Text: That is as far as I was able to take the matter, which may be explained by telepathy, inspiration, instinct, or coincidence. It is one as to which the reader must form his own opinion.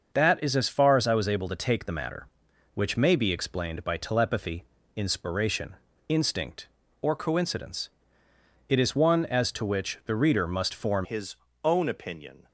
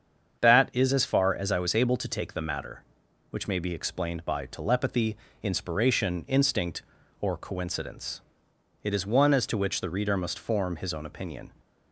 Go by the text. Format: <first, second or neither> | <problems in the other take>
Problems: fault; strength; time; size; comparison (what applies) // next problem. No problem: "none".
second | starts louder than the rest; until 1.1 s; 6.5 dB; strong in the second // changes voice at "his"; from 11.0 s on; 1.4 s long // pauses between "his" and "own"; slight; at 11.3 s; 0.28 s long